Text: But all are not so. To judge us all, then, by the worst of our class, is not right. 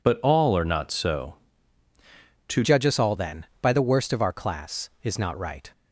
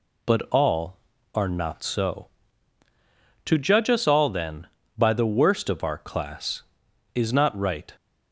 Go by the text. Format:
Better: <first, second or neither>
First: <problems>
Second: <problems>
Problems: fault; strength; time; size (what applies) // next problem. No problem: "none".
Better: second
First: changes voice at "judge"; from 2.6 s on; 3.1 s long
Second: none